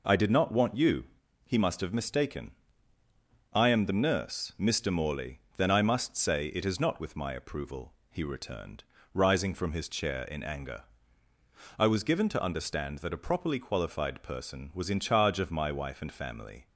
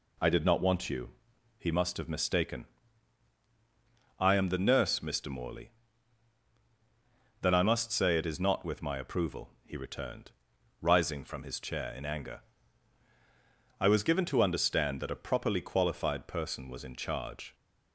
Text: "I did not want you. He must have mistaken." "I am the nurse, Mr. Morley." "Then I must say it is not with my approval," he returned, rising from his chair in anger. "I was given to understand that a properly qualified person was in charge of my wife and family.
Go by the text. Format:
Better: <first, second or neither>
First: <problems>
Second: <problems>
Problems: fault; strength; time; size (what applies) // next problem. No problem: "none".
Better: first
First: none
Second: stops before "of my wife and family"; at 17.5 s